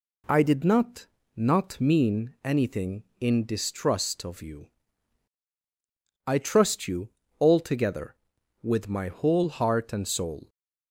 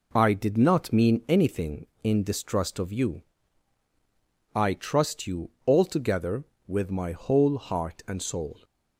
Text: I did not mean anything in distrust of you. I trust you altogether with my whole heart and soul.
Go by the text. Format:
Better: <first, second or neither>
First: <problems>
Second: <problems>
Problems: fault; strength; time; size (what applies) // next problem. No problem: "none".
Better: second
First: says "not" twice; at 1.3 s // pauses between "you" and "altogether"; slight; at 7.0 s; 0.30 s long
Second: none